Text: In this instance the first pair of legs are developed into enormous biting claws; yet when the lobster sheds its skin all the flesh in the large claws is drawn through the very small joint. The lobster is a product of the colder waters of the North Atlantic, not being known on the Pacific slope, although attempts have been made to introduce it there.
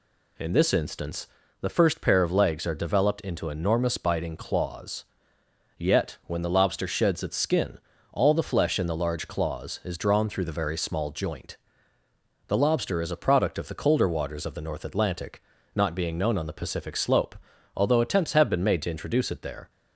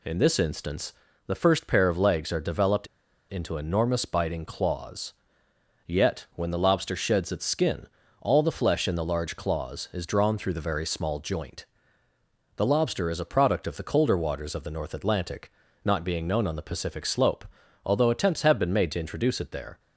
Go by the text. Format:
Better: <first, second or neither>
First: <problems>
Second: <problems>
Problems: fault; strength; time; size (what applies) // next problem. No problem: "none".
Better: first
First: pauses between "instance" and "the"; slight; at 1.2 s; 0.34 s long // pauses between "skin" and "all"; slight; at 7.7 s; 0.32 s long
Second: pauses between "instance" and "the"; slight; at 0.9 s; 0.34 s long // pauses between "developed" and "into"; at 2.8 s; 0.42 s long // pauses between "skin" and "all"; slight; at 7.8 s; 0.32 s long